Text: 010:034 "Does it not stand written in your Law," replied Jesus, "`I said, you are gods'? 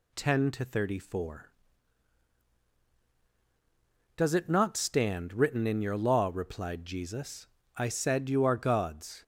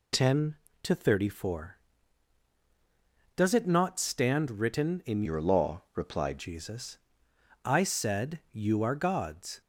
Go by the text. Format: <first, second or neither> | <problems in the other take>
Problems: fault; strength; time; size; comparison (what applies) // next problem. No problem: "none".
first | changes voice from "your" to "replied"; from 5.2 to 6.3 s; 1.1 s long